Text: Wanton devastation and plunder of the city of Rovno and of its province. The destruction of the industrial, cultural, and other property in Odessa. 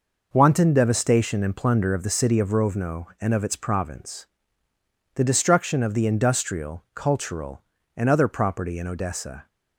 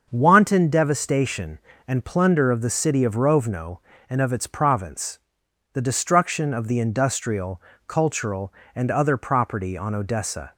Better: first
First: none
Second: starts louder than the rest; until 1.1 s; 6.5 dB // says "on" for "in"; at 9.7 s

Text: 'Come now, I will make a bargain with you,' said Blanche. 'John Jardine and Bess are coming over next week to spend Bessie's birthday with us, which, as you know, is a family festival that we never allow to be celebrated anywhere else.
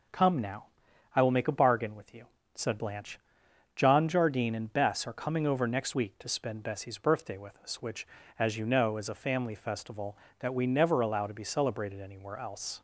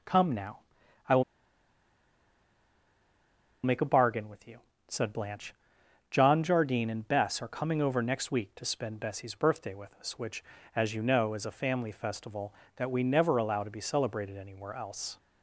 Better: first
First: none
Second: pauses between "will" and "make"; strong; at 1.2 s; 2.4 s long

